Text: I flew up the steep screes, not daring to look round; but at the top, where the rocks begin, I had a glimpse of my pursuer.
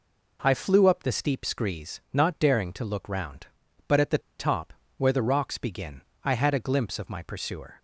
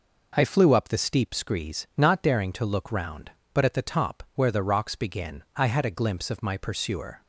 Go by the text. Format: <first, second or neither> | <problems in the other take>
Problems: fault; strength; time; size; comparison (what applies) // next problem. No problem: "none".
second | pauses between "the" and "top"; slight; at 4.2 s; 0.20 s long